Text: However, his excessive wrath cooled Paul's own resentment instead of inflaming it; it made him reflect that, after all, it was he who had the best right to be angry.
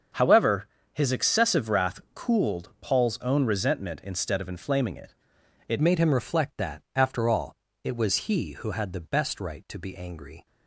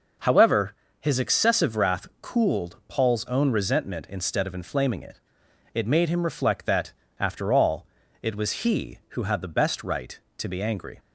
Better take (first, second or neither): second